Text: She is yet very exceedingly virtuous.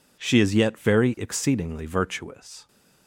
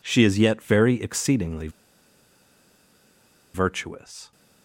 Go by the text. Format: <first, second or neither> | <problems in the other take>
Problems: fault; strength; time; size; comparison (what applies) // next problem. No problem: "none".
first | pauses between "exceedingly" and "virtuous"; strong; at 1.6 s; 1.8 s long